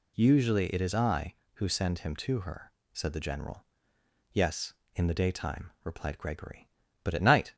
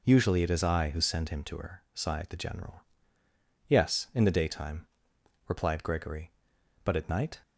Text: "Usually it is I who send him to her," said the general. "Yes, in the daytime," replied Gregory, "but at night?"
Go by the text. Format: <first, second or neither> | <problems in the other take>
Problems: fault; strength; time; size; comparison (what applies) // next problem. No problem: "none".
first | says "sighed" for "said"; at 1.9 s